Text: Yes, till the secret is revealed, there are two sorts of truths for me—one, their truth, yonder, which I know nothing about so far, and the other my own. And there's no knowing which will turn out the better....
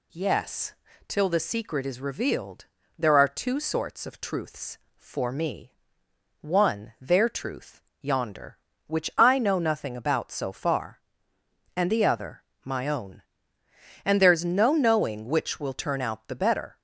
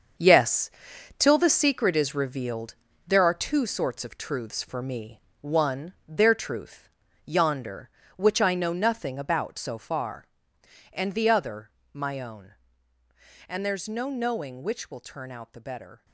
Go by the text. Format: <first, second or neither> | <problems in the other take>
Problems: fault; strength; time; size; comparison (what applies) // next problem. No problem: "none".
first | gets quieter; strong; throughout; 10 dB // pauses between "other" and "my"; slight; at 11.7 s; 0.22 s long; slight in the first